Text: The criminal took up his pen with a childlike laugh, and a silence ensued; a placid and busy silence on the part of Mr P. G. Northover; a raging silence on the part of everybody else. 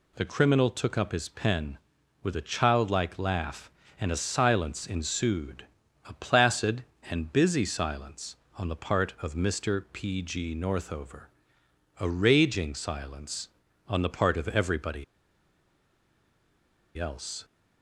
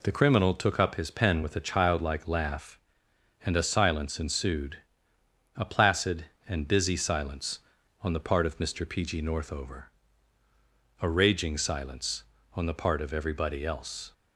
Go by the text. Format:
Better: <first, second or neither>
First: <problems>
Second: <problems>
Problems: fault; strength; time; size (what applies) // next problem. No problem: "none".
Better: second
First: pauses between "everybody" and "else"; strong; at 15.0 s; 1.9 s long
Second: none